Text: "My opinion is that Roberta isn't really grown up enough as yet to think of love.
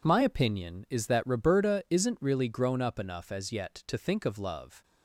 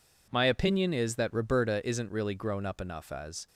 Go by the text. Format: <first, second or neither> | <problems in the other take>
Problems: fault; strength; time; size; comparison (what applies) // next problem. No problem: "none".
first | stops before "yet to think of love"; at 3.4 s